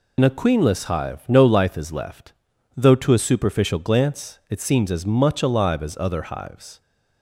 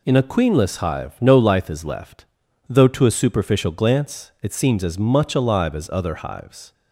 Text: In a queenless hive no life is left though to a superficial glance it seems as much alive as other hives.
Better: second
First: loses the start of "In"; at 0.1 s; 55 ms // pauses between "left" and "though"; at 2.3 s; 0.42 s long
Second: pauses between "left" and "though"; at 2.2 s; 0.42 s long

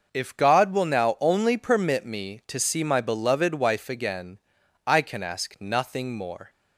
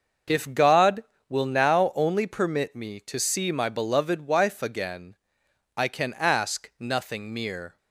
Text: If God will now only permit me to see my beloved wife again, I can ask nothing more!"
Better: first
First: none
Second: starts louder than the rest; noticeable; until 1.5 s; 6 dB // says "mere" for "more"; at 7.3 s

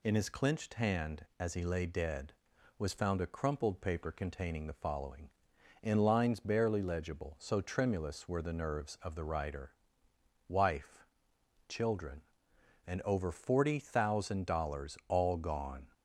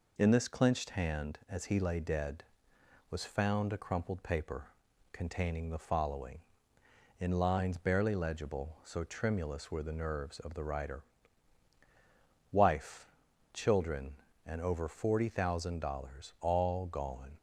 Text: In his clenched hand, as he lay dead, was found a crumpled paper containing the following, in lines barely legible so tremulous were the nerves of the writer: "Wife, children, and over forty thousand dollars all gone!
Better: first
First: none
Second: says "this" for "his"; at 0.2 s // pauses between "paper" and "containing"; noticeable; at 4.6 s; 0.48 s long

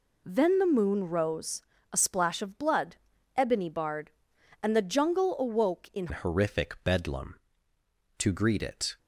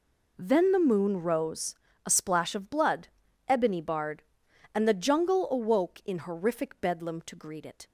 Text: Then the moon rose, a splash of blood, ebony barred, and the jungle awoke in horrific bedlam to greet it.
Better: second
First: changes voice at "horrific"; from 6.1 s on; 2.8 s long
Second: none

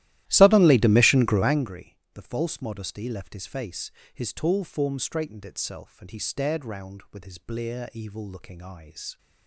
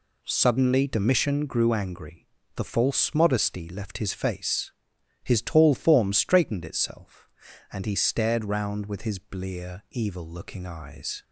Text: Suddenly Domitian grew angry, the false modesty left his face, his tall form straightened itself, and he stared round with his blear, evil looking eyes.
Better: second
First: starts louder than the rest; strong; until 1.7 s; 15 dB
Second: none

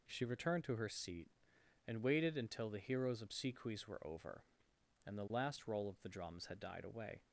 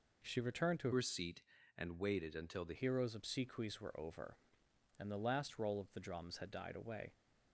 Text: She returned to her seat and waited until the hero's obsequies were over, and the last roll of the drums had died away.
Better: first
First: none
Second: changes voice from "her" to "the"; from 0.9 to 2.7 s; 1.8 s long

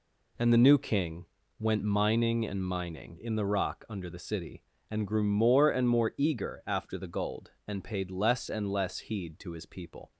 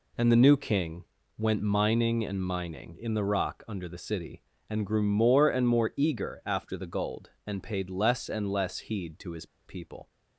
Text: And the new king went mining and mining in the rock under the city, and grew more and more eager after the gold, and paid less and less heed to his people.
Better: first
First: pauses between "king" and "went"; slight; at 1.2 s; 0.34 s long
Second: pauses between "king" and "went"; slight; at 1.0 s; 0.34 s long // pauses between "his" and "people"; slight; at 9.4 s; 0.20 s long

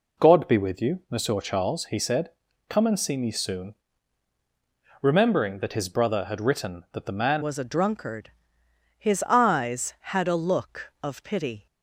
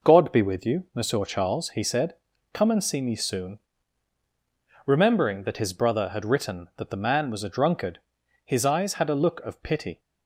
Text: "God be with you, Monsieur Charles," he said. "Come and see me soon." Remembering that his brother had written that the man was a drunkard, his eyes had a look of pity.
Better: second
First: changes voice at "was"; from 7.4 s on; 4.2 s long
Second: none

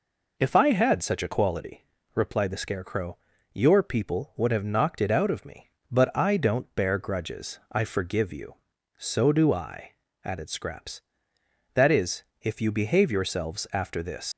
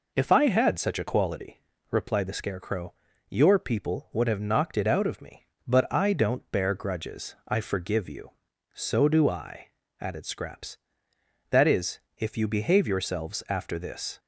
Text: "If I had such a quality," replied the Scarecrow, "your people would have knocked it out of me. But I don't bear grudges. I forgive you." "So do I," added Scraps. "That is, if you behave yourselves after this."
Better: second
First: leaves "this" unfinished; at 14.3 s; 105 ms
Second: none

